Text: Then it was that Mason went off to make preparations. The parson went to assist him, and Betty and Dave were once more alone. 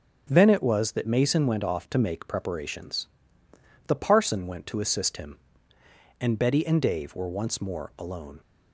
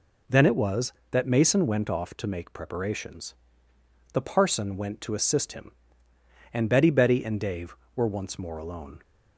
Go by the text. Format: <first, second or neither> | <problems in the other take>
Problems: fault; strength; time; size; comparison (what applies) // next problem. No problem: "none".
first | says "Betty" twice; at 6.8 s